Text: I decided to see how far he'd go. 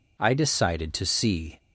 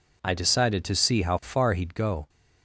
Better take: second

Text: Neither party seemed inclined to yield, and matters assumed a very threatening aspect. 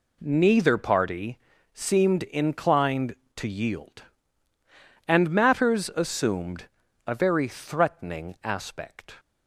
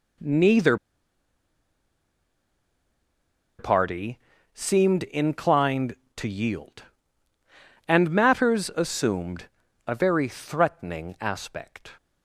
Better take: first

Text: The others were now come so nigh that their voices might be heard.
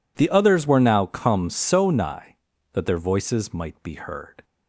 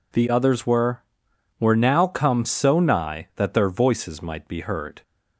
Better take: first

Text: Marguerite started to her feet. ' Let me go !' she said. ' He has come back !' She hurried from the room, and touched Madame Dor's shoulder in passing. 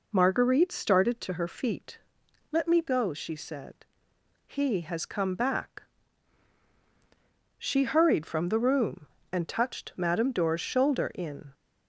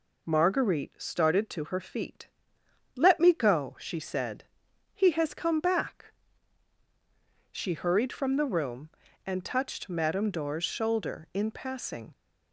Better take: second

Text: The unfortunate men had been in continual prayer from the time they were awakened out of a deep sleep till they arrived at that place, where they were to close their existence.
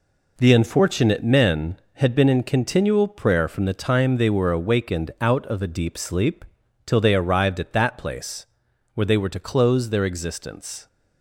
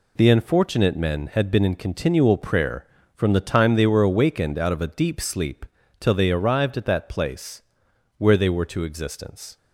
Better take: first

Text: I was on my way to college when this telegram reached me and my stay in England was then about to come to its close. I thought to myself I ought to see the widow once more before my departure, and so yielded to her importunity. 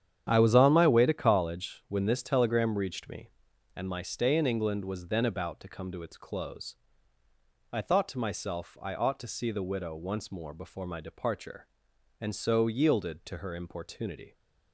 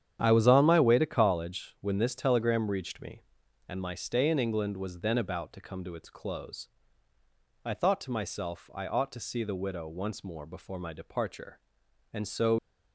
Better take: first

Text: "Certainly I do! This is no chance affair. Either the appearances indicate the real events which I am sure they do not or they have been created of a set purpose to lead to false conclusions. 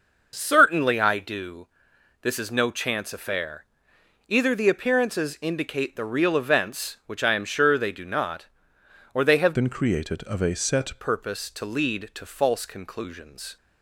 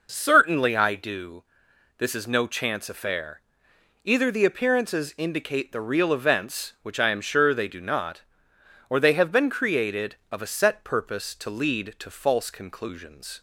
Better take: second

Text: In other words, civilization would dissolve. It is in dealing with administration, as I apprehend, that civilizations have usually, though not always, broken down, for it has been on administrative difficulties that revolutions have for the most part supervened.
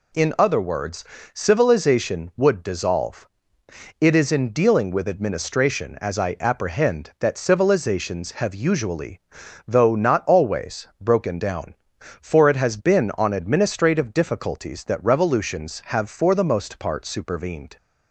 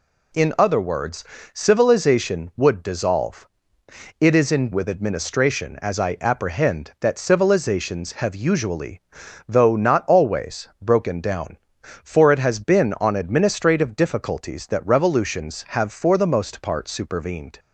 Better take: first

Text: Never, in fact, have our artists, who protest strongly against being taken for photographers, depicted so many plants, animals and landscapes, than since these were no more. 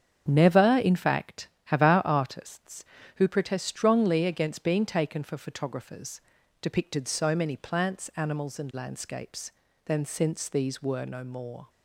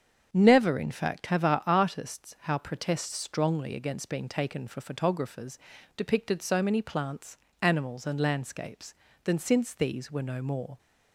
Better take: first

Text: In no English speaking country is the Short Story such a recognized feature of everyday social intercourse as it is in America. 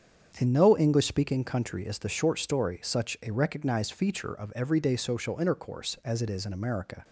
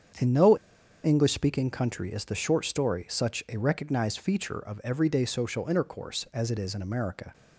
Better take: first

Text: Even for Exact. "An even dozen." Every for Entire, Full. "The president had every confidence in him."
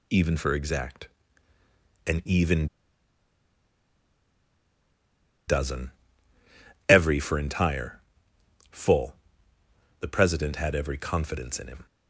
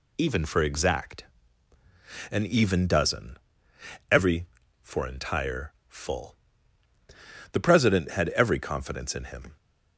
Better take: second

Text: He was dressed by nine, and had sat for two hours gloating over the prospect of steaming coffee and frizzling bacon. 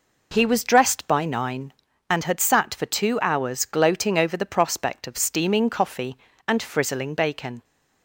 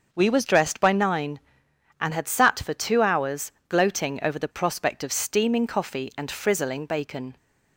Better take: first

